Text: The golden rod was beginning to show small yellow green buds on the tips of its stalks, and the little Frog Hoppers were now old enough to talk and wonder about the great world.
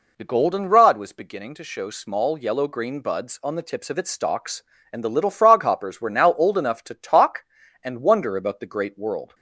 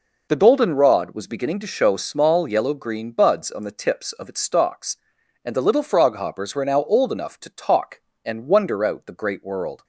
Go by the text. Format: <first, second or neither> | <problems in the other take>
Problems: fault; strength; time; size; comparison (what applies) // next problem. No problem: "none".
first | says "out" for "about"; at 8.8 s